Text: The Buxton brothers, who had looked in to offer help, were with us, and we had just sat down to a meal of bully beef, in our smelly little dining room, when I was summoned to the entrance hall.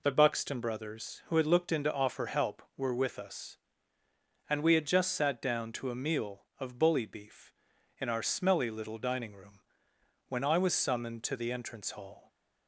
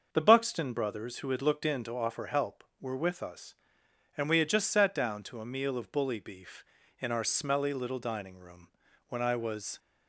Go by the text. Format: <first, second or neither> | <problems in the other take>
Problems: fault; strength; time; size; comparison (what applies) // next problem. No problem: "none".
first | starts louder than the rest; until 1.1 s; 6.5 dB // stops before "summoned to the entrance hall"; at 9.7 s